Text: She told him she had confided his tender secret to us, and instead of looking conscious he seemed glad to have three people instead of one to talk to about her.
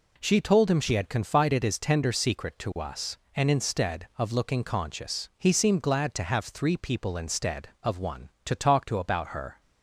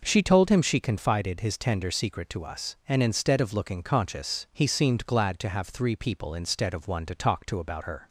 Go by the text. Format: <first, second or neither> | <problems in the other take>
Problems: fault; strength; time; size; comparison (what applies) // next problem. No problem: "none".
first | skips "had"; at 0.8 s